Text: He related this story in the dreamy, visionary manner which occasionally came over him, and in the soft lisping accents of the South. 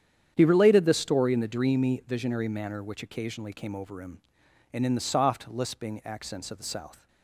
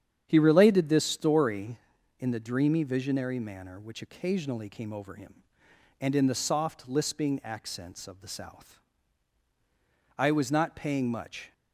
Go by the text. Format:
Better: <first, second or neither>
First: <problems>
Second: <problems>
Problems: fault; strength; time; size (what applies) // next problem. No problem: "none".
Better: first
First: starts louder than the rest; strong; until 1.3 s; 9 dB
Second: starts louder than the rest; strong; until 1.2 s; 8.5 dB // goes on to say "I was not paying much"; from 10.1 s on; 1.3 s long